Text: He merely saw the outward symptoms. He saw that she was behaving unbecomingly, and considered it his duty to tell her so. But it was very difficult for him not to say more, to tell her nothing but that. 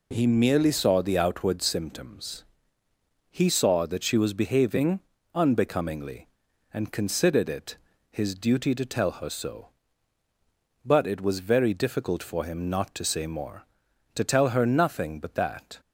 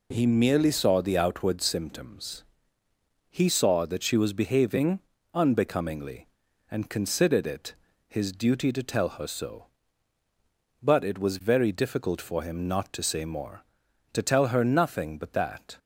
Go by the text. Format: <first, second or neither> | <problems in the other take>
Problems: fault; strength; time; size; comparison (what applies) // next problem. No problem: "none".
neither | pauses between "behaving" and "unbecomingly"; slight; the same in both // pauses between "it" and "his"; slight; the same in both